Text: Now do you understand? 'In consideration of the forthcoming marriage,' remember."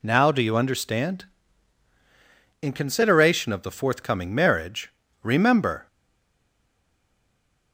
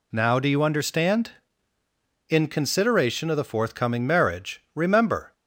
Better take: second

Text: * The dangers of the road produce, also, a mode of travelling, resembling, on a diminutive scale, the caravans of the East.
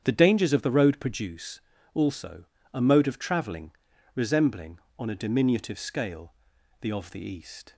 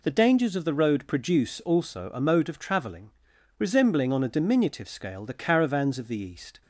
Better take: second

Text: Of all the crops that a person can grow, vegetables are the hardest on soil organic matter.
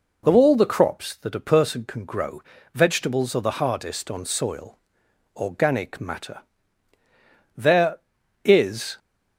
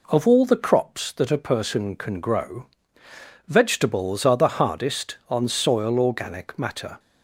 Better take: second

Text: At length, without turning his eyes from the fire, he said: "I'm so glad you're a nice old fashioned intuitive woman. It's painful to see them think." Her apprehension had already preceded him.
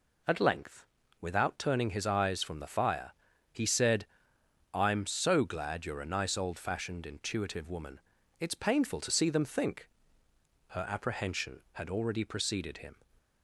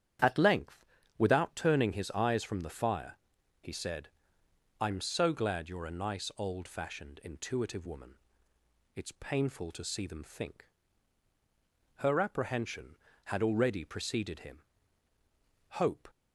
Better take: first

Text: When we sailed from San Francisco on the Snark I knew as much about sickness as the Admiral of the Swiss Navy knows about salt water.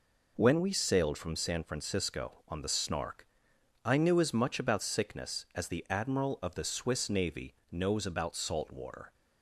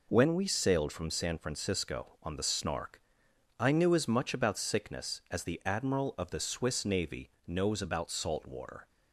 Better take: neither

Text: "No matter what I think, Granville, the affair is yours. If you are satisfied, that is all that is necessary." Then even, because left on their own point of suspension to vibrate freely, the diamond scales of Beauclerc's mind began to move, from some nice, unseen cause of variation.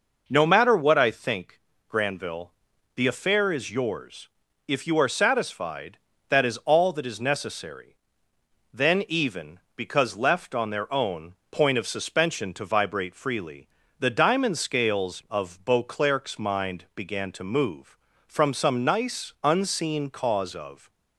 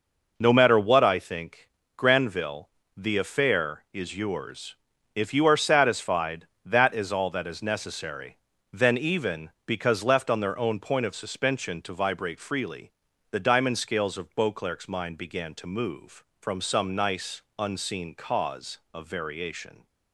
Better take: second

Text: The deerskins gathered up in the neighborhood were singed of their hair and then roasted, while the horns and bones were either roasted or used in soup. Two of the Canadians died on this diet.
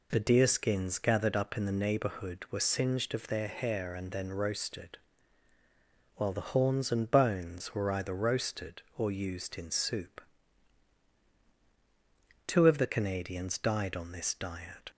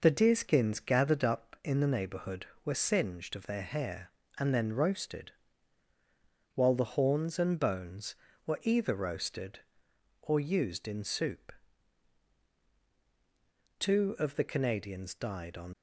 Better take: first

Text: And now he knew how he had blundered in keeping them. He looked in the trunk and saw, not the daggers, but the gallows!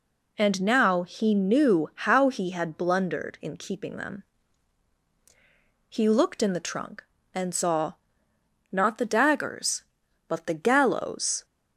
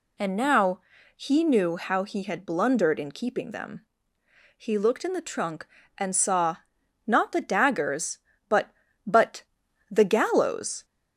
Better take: first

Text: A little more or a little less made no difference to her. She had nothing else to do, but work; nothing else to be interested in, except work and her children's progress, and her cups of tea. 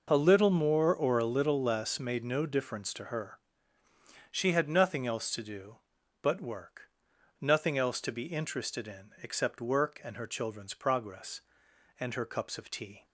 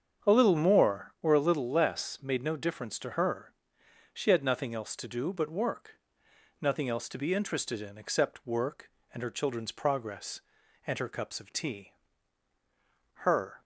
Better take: first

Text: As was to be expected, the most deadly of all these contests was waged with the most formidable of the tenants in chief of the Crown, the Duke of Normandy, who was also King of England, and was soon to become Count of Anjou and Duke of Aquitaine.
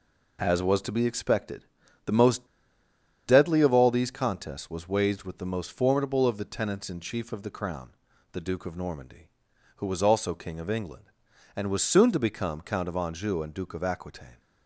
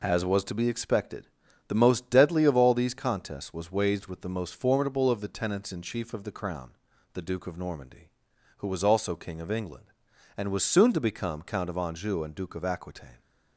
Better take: second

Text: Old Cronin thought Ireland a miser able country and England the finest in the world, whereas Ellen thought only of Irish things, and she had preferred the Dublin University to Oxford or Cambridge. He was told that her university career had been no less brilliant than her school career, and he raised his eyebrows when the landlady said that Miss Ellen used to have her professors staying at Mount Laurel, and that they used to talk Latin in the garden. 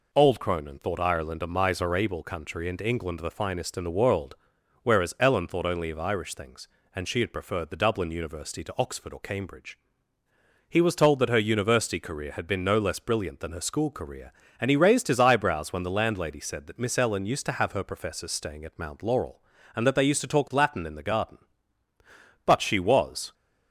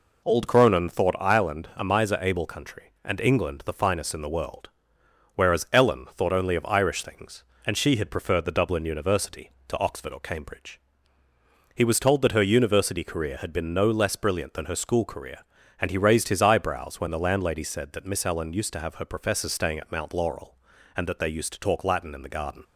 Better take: second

